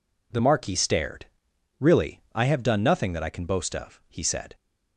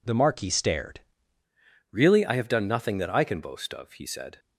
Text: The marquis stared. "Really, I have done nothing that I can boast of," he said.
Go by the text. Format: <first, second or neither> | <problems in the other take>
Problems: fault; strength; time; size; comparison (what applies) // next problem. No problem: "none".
first | changes voice at "Really"; from 1.9 s on; 2.4 s long